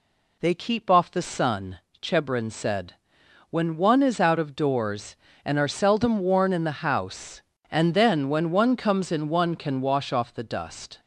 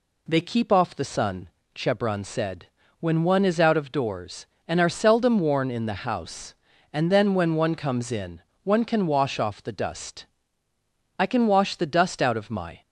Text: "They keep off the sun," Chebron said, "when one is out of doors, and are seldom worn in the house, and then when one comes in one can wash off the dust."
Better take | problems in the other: first | pauses between "in" and "one"; slight; at 8.4 s; 0.24 s long // goes on to say "I can wash the dust out of my"; from 11.1 s on; 1.6 s long

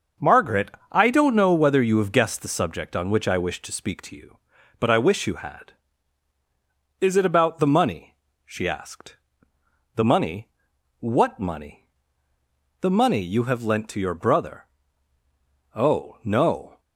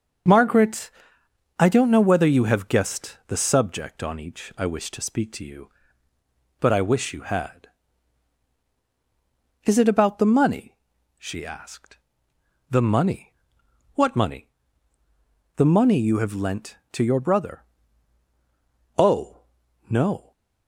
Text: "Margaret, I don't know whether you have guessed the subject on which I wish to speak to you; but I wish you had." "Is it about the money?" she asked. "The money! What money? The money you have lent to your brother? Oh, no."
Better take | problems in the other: first | starts louder than the rest; until 1.9 s; 6 dB; noticeable in the first // says "each" for "which"; at 4.1 s

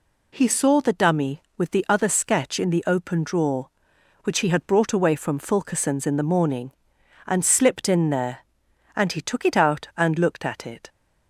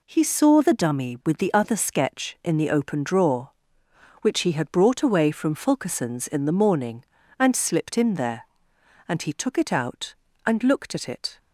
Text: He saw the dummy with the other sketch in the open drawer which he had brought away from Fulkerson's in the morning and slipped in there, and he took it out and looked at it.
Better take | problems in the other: neither | none

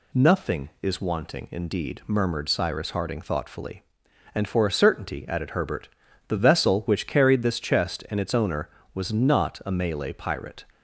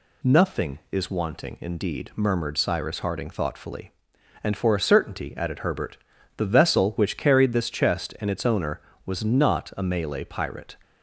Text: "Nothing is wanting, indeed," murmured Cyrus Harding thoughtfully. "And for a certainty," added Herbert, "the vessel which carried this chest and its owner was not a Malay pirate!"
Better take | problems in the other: neither | none

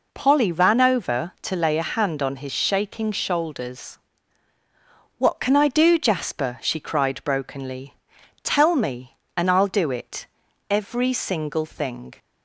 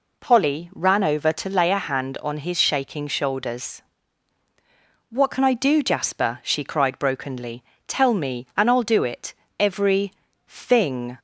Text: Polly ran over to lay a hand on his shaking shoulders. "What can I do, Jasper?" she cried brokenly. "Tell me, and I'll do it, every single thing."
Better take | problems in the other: first | skips "single"; at 10.3 s

